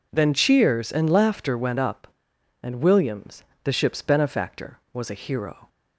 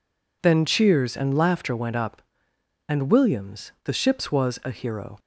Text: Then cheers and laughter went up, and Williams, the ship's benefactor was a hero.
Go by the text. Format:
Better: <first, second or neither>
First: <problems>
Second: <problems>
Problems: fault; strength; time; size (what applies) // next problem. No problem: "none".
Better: first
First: none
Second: skips "benefactor"; at 4.3 s